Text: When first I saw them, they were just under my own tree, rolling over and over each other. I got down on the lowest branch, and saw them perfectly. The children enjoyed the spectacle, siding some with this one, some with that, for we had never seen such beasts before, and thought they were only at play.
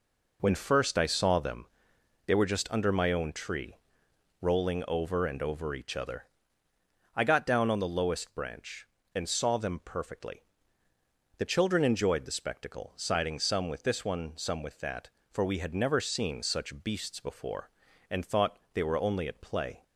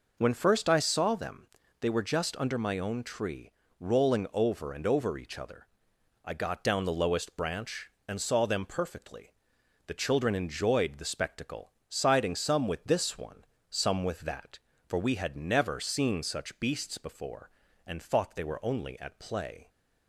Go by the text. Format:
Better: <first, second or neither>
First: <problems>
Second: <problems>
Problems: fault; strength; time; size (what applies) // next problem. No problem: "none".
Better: first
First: none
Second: skips "on"; at 6.8 s